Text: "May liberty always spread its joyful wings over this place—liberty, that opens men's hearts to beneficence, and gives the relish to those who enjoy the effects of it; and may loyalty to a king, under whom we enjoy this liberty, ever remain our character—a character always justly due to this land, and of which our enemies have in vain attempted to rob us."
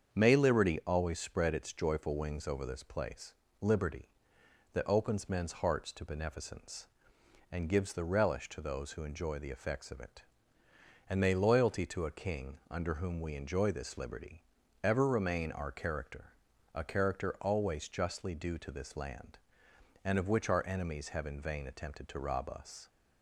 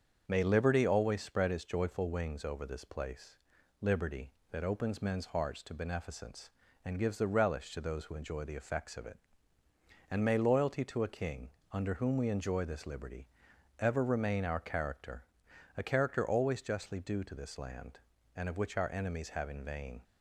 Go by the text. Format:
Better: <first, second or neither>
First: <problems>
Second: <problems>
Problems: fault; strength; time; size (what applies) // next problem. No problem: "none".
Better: first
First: starts louder than the rest; until 1.1 s; 7 dB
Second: starts louder than the rest; until 1.2 s; 7 dB // stops before "attempted to rob us"; at 20.0 s